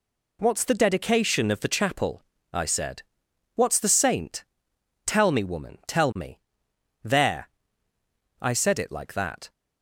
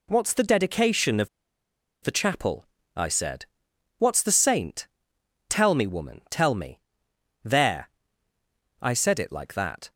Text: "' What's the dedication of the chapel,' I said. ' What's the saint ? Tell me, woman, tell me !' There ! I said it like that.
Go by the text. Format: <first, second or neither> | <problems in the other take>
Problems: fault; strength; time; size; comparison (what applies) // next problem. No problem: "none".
first | pauses between "of" and "the"; noticeable; at 1.2 s; 0.74 s long